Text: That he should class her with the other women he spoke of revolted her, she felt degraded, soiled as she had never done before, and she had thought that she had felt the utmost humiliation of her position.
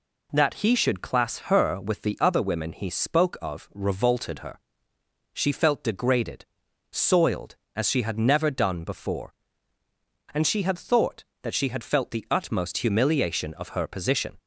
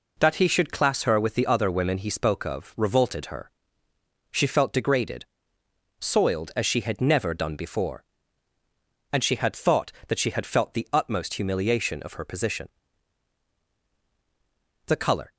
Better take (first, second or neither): first